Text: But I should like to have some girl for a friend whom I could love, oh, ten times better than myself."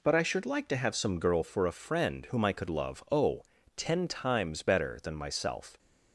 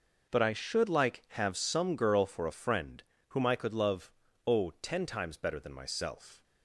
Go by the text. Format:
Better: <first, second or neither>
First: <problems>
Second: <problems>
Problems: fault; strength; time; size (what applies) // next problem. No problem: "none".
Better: first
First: none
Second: skips "to"; at 1.2 s // pauses between "friend" and "whom"; slight; at 3.0 s; 0.26 s long